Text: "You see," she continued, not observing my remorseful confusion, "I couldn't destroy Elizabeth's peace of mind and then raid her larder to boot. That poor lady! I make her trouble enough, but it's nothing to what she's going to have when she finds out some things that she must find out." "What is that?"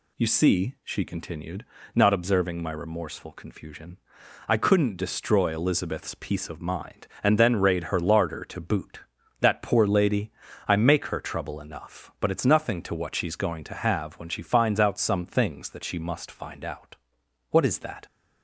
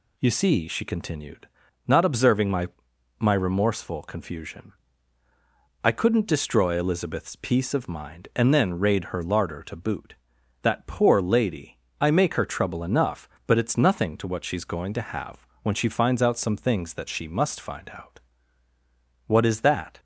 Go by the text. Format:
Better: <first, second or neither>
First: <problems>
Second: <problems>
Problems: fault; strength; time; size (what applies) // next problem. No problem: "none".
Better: first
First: none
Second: says "my" twice; at 3.1 s // pauses between "have" and "when"; slight; at 15.4 s; 0.18 s long